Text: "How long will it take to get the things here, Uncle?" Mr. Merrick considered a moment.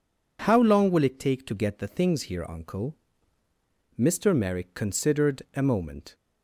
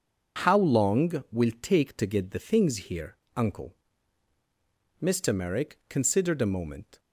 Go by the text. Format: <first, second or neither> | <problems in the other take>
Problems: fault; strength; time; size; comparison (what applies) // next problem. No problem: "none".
first | skips "it"; at 1.5 s